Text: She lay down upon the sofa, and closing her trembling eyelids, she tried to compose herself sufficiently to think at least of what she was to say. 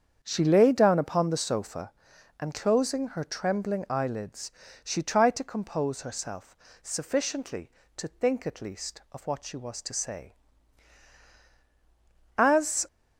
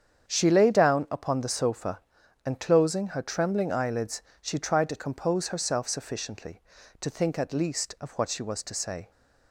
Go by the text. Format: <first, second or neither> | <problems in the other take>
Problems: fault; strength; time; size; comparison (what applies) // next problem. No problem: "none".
second | starts louder than the rest; strong; until 1.2 s; 7.5 dB; strong in the second // pauses between "herself" and "sufficiently"; slight; at 6.5 s; 0.24 s long // goes on to say "As"; from 12.3 s on; 0.50 s long